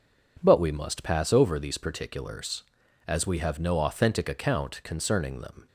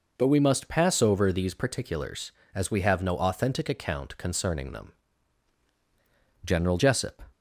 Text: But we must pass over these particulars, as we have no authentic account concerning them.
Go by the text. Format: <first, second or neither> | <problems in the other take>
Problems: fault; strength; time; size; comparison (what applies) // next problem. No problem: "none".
first | goes on to say "General Jessup"; noticeable; from 6.4 s on; 0.80 s long